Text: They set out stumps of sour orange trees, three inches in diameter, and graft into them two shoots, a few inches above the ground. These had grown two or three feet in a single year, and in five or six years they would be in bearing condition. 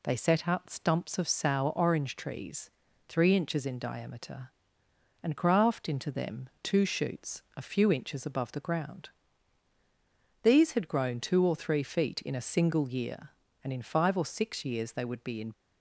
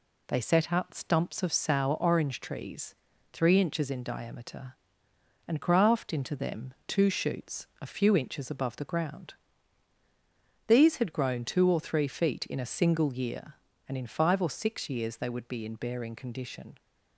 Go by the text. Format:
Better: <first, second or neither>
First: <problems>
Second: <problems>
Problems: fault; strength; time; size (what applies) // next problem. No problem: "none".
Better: second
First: pauses between "them" and "two"; slight; at 6.4 s; 0.16 s long // stops before "bearing condition"; at 15.5 s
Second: pauses between "them" and "two"; slight; at 6.7 s; 0.16 s long